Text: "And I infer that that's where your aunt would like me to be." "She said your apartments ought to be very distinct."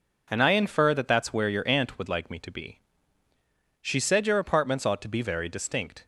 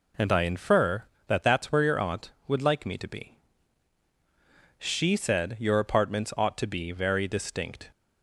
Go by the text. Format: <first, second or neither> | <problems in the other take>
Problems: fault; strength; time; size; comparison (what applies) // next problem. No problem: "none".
neither | none